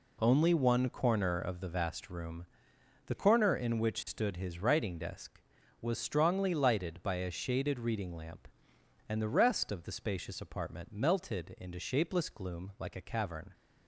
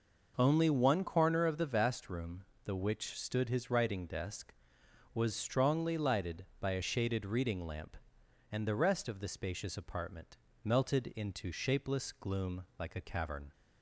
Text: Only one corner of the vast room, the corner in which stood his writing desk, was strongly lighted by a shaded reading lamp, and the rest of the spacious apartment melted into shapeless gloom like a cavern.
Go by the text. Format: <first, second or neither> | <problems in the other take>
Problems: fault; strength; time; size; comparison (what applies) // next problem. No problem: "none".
first | skips "corner in"; at 2.7 s // pauses between "apartment" and "melted"; slight; at 10.3 s; 0.28 s long // pauses between "gloom" and "like"; slight; at 12.6 s; 0.16 s long